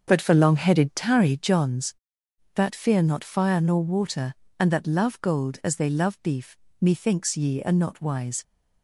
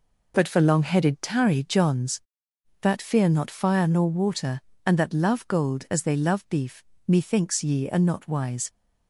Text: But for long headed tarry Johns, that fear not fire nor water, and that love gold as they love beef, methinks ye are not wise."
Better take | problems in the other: second | starts louder than the rest; until 1.4 s; 6 dB

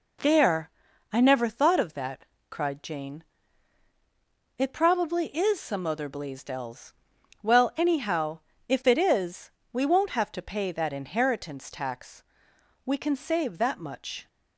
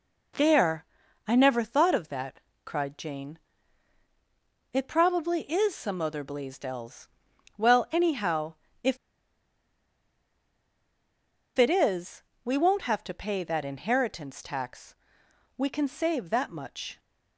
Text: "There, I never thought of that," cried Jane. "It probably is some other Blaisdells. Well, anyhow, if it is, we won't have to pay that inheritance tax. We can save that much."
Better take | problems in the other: first | pauses between "if" and "it"; strong; at 8.9 s; 2.5 s long

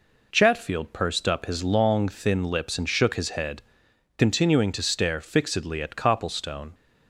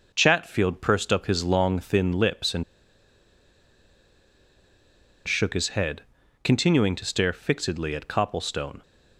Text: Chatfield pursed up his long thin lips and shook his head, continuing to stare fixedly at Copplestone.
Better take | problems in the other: first | pauses between "and" and "shook"; strong; at 2.6 s; 2.6 s long

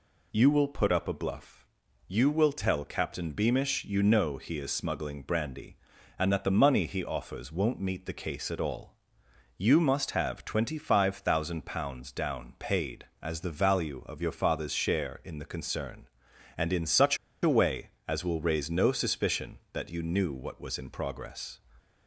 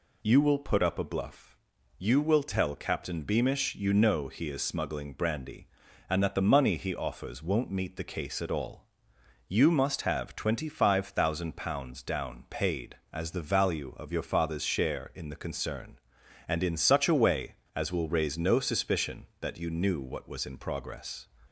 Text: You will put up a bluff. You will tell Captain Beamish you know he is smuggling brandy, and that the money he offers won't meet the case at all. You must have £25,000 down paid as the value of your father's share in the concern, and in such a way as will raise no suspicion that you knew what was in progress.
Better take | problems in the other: second | pauses between "such" and "a"; slight; at 17.1 s; 0.26 s long

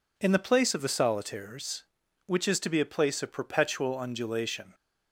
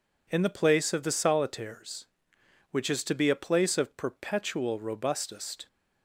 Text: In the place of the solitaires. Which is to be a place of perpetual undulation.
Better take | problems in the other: first | says "robustest" for "undulation"; at 4.7 s

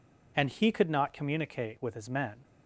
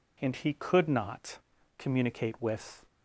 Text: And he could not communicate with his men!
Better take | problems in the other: first | pauses between "not" and "communicate"; at 1.3 s; 0.38 s long // stops before "his men"; at 2.8 s

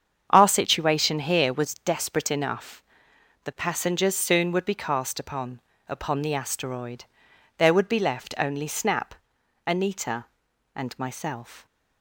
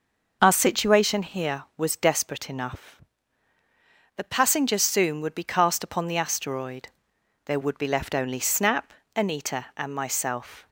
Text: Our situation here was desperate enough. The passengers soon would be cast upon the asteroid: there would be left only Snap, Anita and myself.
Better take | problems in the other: second | starts louder than the rest; strong; until 1.3 s; 7.5 dB // says "upon" twice; at 5.8 s

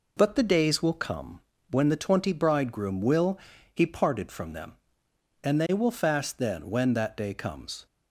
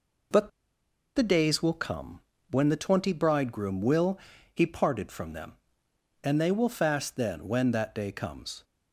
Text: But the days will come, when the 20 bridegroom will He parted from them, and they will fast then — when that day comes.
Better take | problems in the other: first | pauses between "But" and "the"; noticeable; at 0.4 s; 0.67 s long // pauses between "will" and "He"; slight; at 4.1 s; 0.34 s long; slight in the first

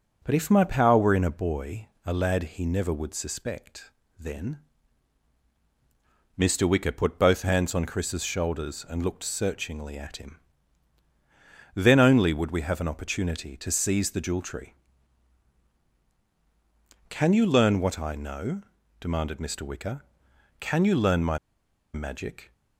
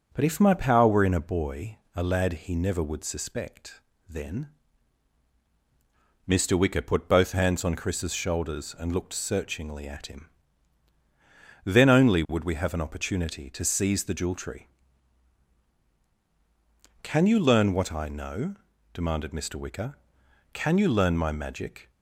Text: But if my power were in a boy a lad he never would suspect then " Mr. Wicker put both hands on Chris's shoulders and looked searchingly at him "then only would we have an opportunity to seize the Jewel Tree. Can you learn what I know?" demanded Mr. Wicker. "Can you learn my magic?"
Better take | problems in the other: second | starts louder than the rest; until 1.2 s; 7 dB; also in the second // pauses between "boy" and "a"; slight; at 1.8 s; 0.18 s long; slight in the second // pauses between "suspect" and "then"; slight; at 3.9 s; 0.26 s long; slight in the second // pauses between "him" and "then"; strong; at 10.3 s; 1.3 s long; strong in the second // pauses between "my" and "magic"; noticeable; at 21.3 s; 0.56 s long

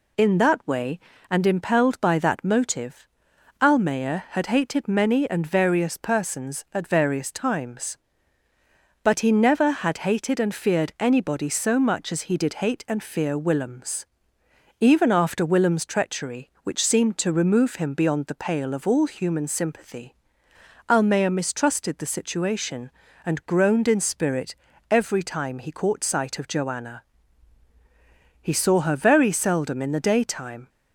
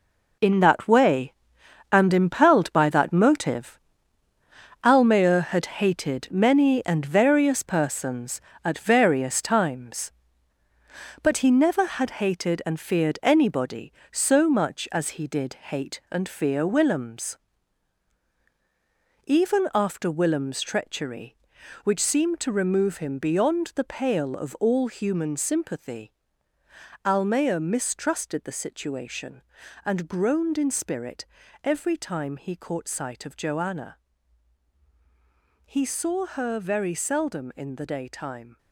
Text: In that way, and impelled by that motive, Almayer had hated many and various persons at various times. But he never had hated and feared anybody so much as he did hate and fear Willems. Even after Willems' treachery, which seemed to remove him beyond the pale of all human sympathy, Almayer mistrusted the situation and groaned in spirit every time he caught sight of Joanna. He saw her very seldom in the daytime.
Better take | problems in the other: first | gets quieter; strong; throughout; 10 dB // pauses between "spirit" and "every"; at 31.2 s; 0.38 s long; slight in the first

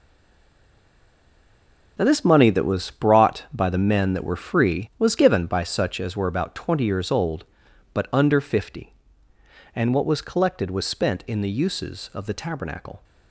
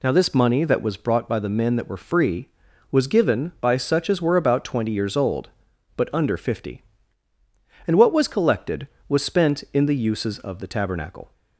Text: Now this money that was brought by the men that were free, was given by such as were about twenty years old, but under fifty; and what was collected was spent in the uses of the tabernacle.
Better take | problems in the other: second | stays silent before the first word; noticeable; until 1.9 s; 1.9 s long

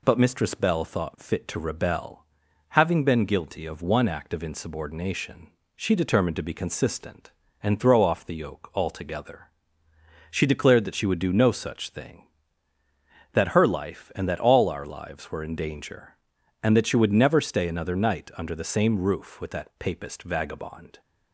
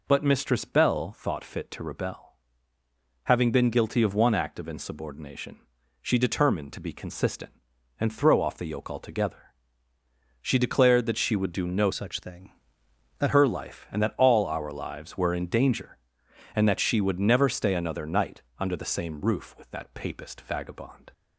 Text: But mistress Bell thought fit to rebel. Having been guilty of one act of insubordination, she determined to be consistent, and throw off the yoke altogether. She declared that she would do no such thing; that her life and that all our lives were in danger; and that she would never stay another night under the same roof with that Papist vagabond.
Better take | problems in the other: first | changes voice from "such" to "that"; from 11.9 to 13.3 s; 1.4 s long // pauses between "night" and "under"; slight; at 18.4 s; 0.18 s long

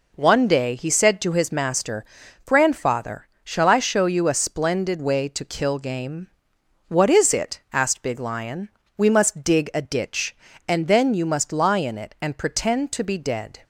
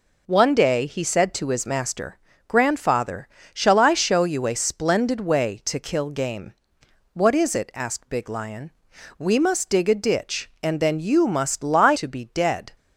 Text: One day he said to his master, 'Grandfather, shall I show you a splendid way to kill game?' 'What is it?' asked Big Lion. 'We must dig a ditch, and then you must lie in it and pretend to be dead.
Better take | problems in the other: first | skips "in it and pretend"; at 11.9 s

